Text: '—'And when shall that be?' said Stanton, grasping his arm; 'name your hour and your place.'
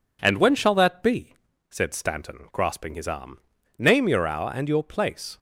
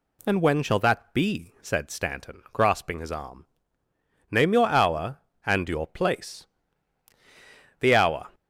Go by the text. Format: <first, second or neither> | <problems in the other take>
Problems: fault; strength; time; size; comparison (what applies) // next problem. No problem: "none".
first | goes on to say "The hour"; from 7.7 s on; 0.50 s long